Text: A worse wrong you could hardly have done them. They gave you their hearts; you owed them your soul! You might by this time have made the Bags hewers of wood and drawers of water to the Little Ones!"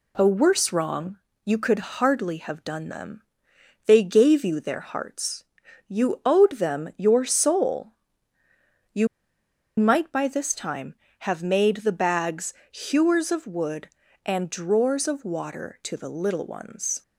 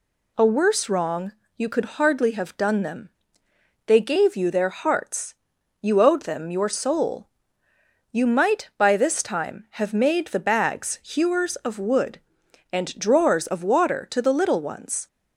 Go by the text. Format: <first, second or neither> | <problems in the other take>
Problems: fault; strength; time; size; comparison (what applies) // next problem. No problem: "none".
second | pauses between "wrong" and "you"; slight; at 1.1 s; 0.26 s long; slight in the second // pauses between "You" and "might"; noticeable; at 9.0 s; 0.72 s long // pauses between "Bags" and "hewers"; slight; at 12.5 s; 0.16 s long